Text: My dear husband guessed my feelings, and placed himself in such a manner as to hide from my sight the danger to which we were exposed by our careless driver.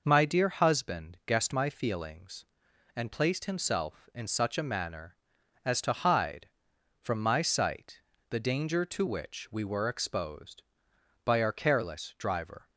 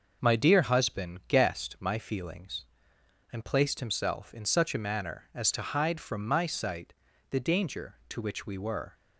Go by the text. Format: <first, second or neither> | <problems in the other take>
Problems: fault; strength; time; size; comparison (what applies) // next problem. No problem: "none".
first | pauses between "sight" and "the"; at 6.9 s; 0.38 s long; slight in the first // stops before "exposed by our careless driver"; at 8.9 s